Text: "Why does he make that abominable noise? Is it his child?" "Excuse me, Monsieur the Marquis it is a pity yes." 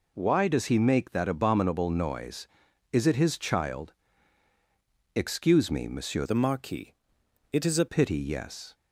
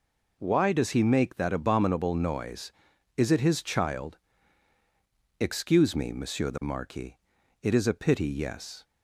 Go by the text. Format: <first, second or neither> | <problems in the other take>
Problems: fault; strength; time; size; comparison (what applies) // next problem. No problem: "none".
second | changes voice from "the" to "a"; from 6.2 to 7.8 s; 1.6 s long // pauses between "Marquis" and "it"; noticeable; at 6.9 s; 0.60 s long; noticeable in the second